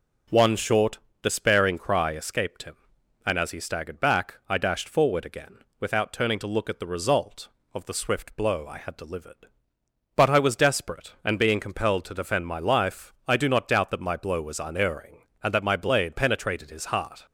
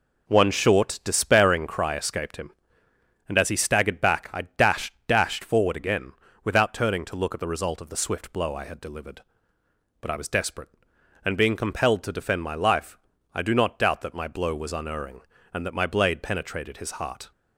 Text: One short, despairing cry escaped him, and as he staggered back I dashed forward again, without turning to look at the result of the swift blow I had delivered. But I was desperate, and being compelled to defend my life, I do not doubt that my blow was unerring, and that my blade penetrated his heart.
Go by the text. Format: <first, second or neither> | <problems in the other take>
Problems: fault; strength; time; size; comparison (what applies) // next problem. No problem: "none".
first | says "dashed" twice; at 5.0 s